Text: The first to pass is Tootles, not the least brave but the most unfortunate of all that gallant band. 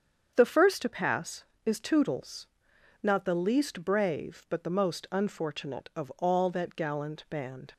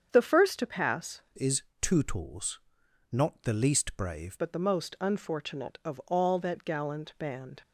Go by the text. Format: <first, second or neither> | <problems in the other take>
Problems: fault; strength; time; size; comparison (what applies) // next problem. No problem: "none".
first | starts louder than the rest; strong; until 1.1 s; 7.5 dB; strong in the first // changes voice from "is" to "brave"; from 1.3 to 4.3 s; 3.0 s long // pauses between "is" and "Tootles"; slight; at 1.6 s; 0.18 s long